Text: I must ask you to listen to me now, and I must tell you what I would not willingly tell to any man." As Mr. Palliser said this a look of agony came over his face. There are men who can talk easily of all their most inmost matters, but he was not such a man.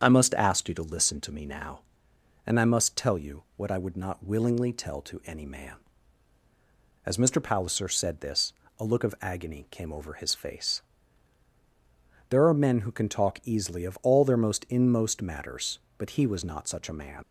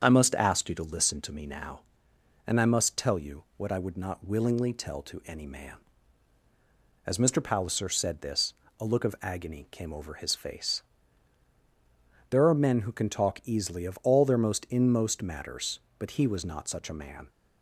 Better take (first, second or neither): second